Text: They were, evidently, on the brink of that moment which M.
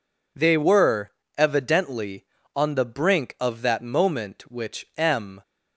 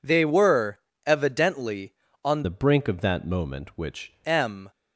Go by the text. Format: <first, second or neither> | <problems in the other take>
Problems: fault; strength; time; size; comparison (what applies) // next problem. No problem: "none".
first | changes voice from "the" to "which"; from 2.4 to 4.1 s; 1.7 s long